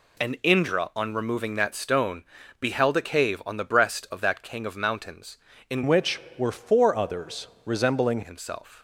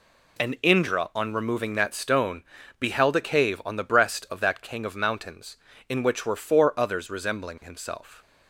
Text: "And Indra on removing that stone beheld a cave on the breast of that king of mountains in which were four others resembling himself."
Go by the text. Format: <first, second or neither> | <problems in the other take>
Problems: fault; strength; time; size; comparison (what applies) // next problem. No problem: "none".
second | pauses between "stone" and "beheld"; slight; at 2.2 s; 0.34 s long; slight in the second // changes voice from "which" to "resembling"; from 5.8 to 8.1 s; 2.3 s long // pauses between "others" and "resembling"; slight; at 7.4 s; 0.16 s long